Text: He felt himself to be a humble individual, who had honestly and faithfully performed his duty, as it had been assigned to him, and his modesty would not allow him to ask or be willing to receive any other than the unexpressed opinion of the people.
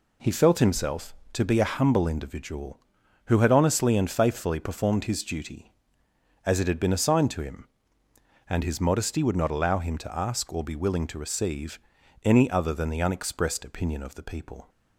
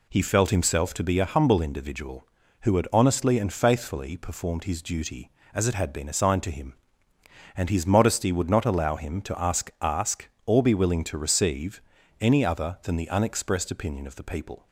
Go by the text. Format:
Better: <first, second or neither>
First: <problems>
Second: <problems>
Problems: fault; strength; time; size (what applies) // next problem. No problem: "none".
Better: first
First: pauses between "receive" and "any"; at 11.7 s; 0.44 s long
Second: says "ask" twice; at 9.8 s // pauses between "receive" and "any"; at 11.8 s; 0.40 s long